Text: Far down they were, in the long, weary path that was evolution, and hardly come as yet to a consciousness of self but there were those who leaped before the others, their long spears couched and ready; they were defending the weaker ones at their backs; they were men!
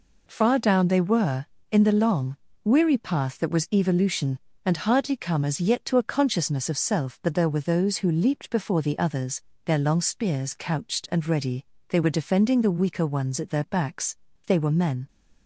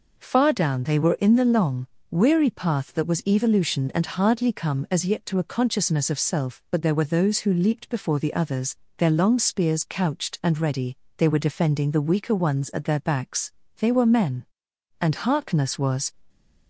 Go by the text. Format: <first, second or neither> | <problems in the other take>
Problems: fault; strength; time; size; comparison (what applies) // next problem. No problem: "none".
first | goes on to say "And Harkness was"; noticeable; from 14.9 s on; 1.1 s long